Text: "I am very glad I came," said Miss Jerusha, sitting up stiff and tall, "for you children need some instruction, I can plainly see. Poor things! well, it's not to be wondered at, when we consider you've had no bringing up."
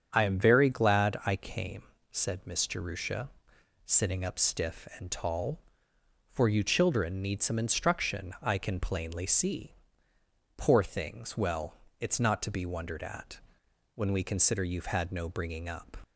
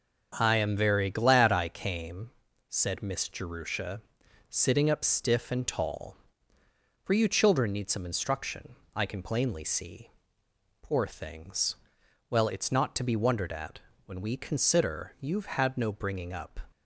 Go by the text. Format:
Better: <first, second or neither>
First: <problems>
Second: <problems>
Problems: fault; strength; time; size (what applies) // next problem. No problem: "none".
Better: neither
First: starts louder than the rest; until 1.1 s; 7 dB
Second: starts louder than the rest; until 1.4 s; 7 dB